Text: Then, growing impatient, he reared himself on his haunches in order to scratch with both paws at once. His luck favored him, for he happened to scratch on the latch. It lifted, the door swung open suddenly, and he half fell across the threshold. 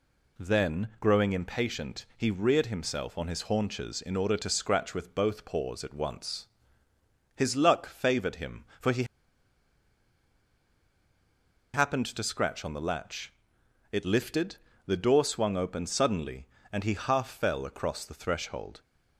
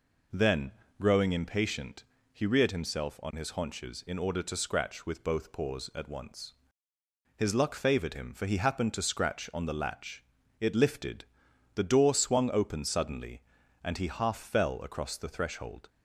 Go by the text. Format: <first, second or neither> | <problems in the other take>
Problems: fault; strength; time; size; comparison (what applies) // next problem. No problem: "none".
second | pauses between "he" and "happened"; strong; at 9.0 s; 2.6 s long